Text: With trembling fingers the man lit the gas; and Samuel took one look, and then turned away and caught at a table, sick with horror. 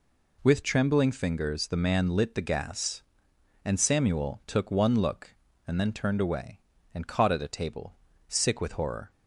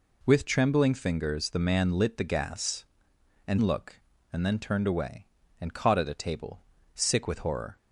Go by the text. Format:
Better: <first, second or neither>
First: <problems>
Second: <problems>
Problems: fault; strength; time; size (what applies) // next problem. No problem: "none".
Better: first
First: none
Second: skips "Samuel took one"; at 3.6 s